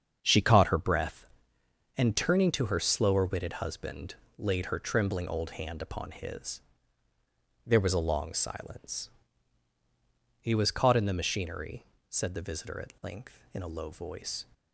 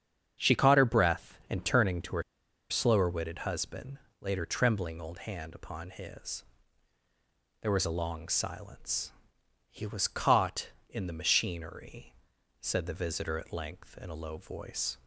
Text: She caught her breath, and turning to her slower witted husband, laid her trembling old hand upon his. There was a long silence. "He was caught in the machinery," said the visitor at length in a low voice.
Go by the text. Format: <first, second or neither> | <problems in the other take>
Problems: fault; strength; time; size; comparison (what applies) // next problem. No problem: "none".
first | starts louder than the rest; strong; until 1.5 s; 8 dB; strong in the first // pauses between "her" and "slower"; noticeable; at 2.2 s; 0.47 s long